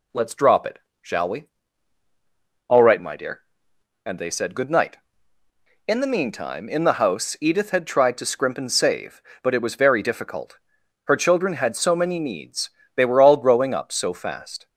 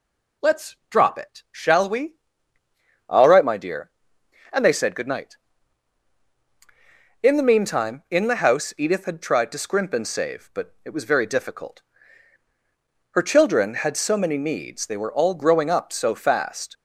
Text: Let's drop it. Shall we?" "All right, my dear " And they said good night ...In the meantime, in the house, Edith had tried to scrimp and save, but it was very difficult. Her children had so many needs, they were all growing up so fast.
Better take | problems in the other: neither | none

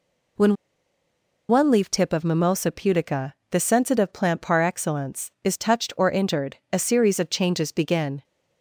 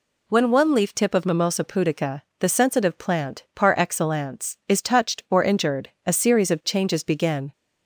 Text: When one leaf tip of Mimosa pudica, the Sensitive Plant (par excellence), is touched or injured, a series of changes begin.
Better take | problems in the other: second | pauses between "When" and "one"; noticeable; at 0.5 s; 0.95 s long

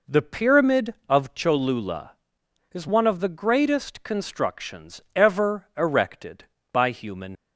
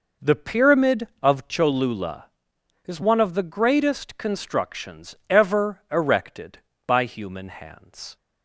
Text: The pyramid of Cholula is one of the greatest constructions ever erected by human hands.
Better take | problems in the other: second | pauses between "constructions" and "ever"; slight; at 4.9 s; 0.16 s long; slight in the second // stops before "hands"; at 7.3 s

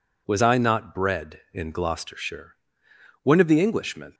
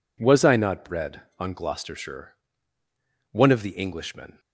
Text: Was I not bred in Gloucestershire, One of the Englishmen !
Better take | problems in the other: first | says "on" for "in"; at 1.3 s

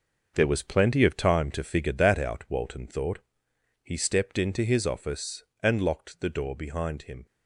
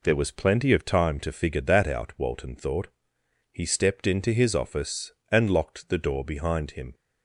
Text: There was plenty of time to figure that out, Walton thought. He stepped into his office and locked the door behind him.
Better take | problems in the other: second | gets quieter; strong; throughout; 10 dB

